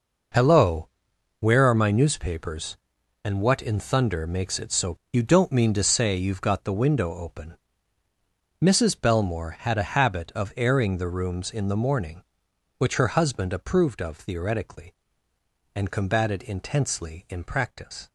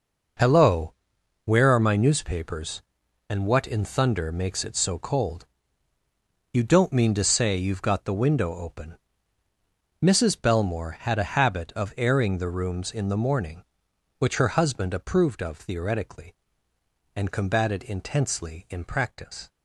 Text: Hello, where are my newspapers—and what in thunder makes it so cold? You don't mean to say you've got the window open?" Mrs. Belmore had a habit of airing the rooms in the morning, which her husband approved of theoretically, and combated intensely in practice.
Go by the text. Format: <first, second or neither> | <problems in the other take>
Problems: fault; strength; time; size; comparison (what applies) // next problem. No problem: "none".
second | skips "cold"; at 5.0 s